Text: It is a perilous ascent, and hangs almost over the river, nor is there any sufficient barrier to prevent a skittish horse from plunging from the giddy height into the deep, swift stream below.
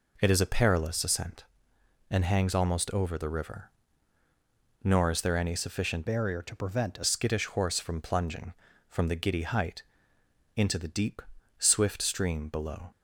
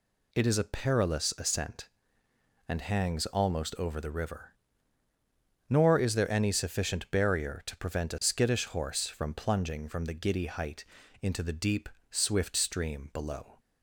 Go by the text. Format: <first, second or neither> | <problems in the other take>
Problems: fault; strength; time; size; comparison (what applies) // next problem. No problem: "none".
second | changes voice from "barrier" to "a"; from 6.0 to 7.0 s; 1.0 s long // pauses between "height" and "into"; noticeable; at 9.8 s; 0.74 s long; also in the second